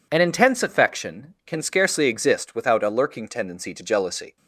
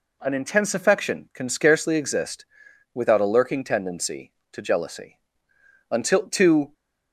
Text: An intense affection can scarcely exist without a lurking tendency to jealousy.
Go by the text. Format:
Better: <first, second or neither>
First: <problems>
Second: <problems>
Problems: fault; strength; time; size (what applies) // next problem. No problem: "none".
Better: first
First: none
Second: pauses between "exist" and "without"; noticeable; at 2.4 s; 0.50 s long // goes on to say "Until to"; noticeable; from 5.9 s on; 0.82 s long